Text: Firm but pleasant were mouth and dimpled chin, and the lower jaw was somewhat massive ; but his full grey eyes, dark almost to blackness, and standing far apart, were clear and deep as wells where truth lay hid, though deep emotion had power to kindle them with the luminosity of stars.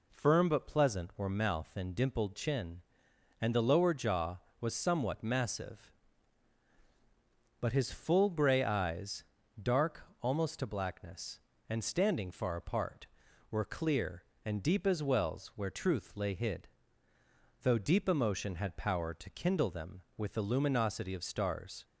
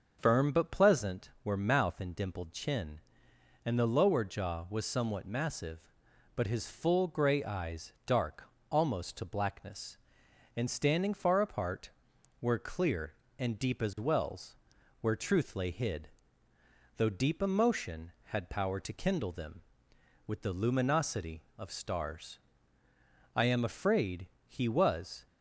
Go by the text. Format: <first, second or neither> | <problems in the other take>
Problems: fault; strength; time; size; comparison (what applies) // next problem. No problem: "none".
first | starts louder than the rest; noticeable; until 1.2 s; 6 dB // pauses between "dark" and "almost"; slight; at 8.4 s; 0.26 s long; slight in the first // pauses between "wells" and "where"; noticeable; at 14.5 s; 0.46 s long // goes on to say "I am afraid he was"; strong; from 23.3 s on; 1.9 s long